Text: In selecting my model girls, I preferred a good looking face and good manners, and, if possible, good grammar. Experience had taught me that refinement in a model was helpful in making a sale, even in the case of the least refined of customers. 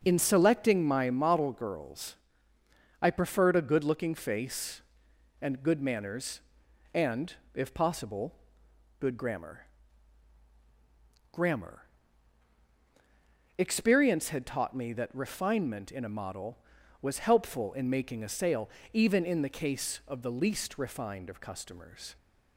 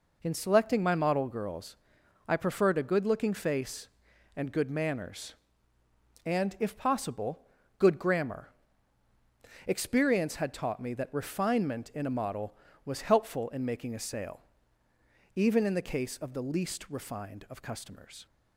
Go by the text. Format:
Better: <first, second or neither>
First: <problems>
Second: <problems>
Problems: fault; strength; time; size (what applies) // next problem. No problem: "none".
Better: second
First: says "grammar" twice; at 11.3 s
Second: none